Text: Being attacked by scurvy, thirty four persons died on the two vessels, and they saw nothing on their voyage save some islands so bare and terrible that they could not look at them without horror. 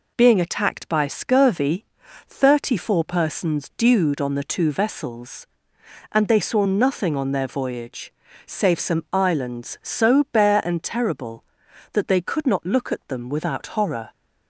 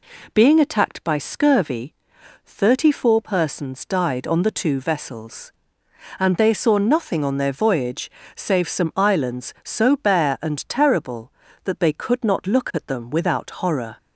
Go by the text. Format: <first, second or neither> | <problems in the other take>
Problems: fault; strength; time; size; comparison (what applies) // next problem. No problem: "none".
second | says "dewed" for "died"; at 3.7 s // pauses between "voyage" and "save"; slight; at 8.1 s; 0.35 s long; slight in the second